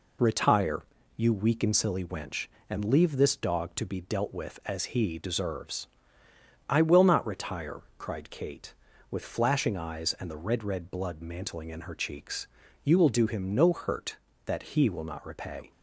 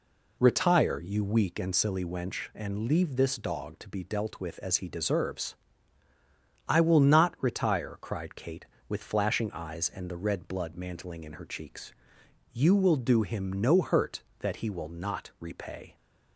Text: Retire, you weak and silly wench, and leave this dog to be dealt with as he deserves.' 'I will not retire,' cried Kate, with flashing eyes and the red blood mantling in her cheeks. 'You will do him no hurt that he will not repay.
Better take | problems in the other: second | says "red" twice; at 10.6 s

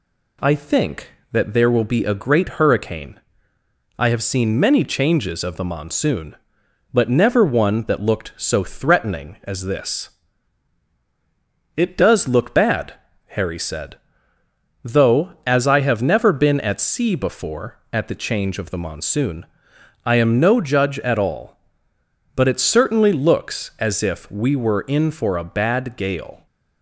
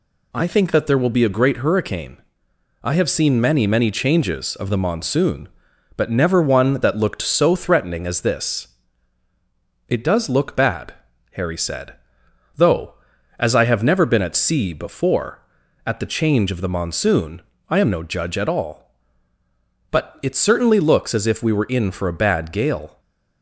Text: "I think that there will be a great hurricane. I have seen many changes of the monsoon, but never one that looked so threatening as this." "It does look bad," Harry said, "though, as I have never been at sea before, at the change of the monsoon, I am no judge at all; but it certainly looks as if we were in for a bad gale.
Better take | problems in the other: first | says "many" twice; at 3.6 s // stays silent after the last word; slight; from 22.9 s on; 0.5 s long

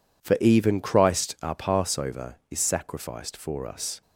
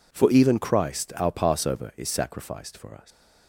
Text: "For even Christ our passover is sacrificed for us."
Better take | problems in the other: first | leaves "us" unfinished; at 3.1 s; 120 ms

